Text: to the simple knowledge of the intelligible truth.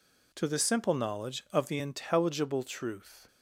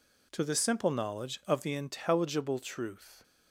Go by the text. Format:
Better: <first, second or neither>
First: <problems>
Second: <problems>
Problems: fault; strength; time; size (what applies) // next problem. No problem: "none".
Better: neither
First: none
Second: none